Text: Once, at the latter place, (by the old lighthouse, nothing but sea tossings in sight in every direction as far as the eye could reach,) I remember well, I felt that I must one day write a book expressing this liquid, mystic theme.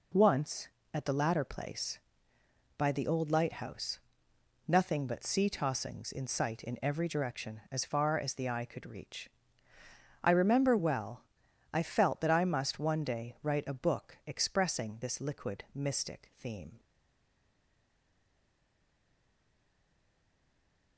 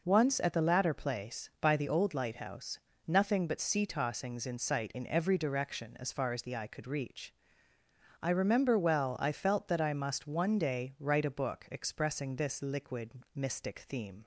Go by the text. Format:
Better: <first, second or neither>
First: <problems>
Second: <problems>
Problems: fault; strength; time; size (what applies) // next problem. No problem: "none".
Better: second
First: stays silent after the last word; strong; from 16.7 s on; 4.2 s long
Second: none